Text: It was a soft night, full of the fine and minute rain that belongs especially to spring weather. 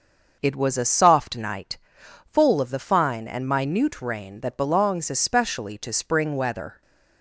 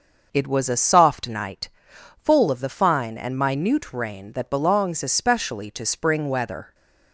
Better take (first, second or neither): neither